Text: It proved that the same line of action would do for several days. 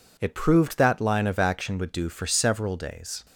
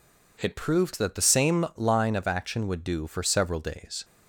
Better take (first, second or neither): second